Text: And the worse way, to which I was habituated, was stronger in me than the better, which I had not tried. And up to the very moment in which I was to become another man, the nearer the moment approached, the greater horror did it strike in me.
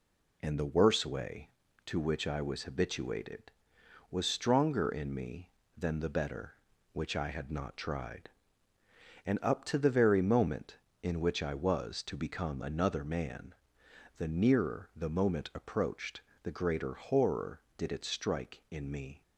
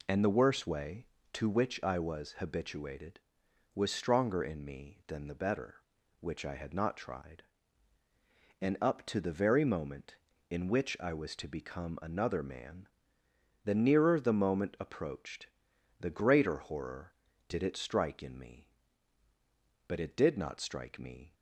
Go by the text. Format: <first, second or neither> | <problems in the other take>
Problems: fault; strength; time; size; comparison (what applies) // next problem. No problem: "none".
first | goes on to say "But it did not strike me"; from 19.8 s on; 1.4 s long